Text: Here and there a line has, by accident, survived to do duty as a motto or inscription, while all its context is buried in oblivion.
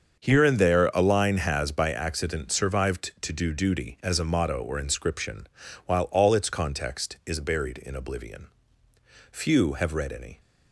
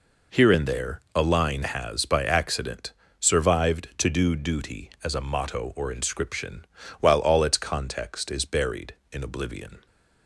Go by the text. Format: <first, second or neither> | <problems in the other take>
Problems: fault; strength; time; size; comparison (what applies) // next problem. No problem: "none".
second | starts louder than the rest; until 1.2 s; 7 dB // goes on to say "Few have read any"; noticeable; from 9.3 s on; 1.0 s long